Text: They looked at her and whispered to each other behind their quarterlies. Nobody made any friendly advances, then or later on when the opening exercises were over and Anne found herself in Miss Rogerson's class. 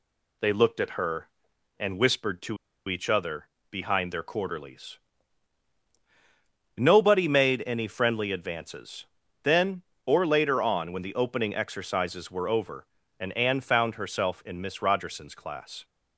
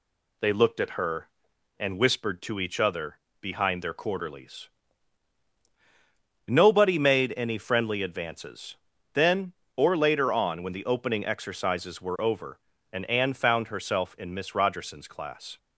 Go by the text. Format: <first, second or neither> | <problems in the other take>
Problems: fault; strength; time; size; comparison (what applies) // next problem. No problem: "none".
second | pauses between "to" and "each"; slight; at 2.5 s; 0.31 s long // pauses between "other" and "behind"; slight; at 3.4 s; 0.22 s long; slight in the second